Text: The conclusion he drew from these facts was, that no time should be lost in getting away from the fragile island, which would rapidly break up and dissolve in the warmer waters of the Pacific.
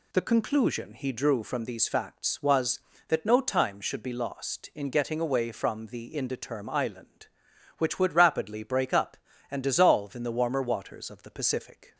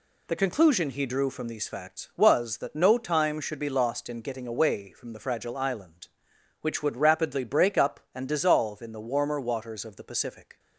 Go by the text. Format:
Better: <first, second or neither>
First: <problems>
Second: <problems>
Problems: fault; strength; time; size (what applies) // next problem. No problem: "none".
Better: second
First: says "indeterm" for "fragile"; at 6.1 s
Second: none